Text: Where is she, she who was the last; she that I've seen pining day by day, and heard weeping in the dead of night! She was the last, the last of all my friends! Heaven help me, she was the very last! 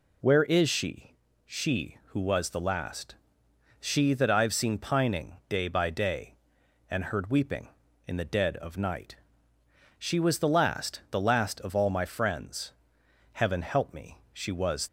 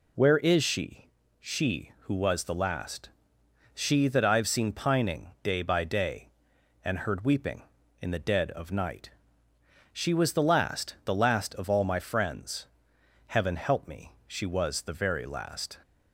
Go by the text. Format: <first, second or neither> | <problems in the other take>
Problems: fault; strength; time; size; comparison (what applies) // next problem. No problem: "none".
second | stops before "the very last"; at 14.8 s